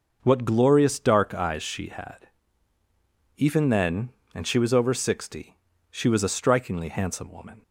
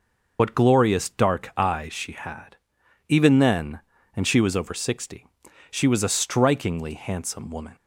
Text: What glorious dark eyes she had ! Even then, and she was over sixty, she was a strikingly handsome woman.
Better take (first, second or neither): first